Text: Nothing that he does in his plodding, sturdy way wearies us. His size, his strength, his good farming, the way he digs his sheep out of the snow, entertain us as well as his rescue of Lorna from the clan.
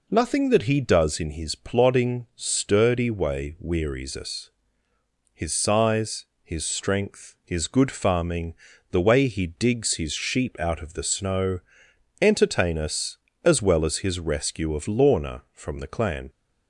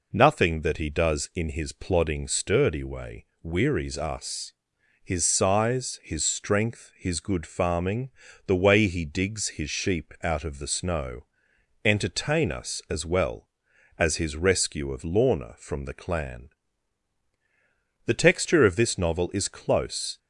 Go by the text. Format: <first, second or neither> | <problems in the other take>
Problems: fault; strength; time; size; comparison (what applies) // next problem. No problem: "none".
first | pauses between "way" and "wearies"; slight; at 3.2 s; 0.16 s long // goes on to say "The texture of this novel is close"; strong; from 18.0 s on; 2.1 s long